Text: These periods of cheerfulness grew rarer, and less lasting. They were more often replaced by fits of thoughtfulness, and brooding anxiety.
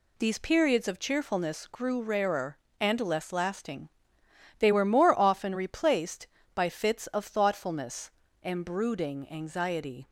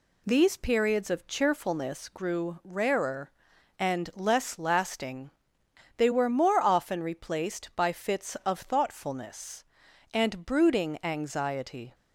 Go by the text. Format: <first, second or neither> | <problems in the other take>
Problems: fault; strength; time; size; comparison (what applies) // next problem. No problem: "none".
neither | none